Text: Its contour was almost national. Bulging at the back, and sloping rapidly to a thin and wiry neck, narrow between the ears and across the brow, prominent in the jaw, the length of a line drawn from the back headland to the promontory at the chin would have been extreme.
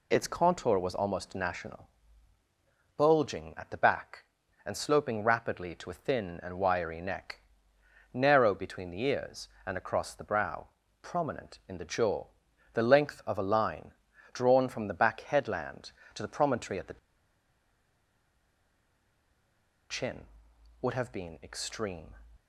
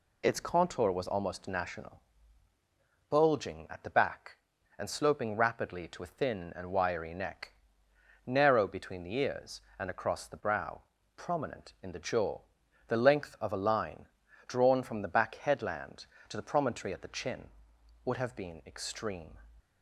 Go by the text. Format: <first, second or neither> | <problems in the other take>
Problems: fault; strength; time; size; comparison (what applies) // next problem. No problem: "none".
second | pauses between "line" and "drawn"; at 13.9 s; 0.40 s long; also in the second // pauses between "the" and "chin"; strong; at 16.9 s; 2.9 s long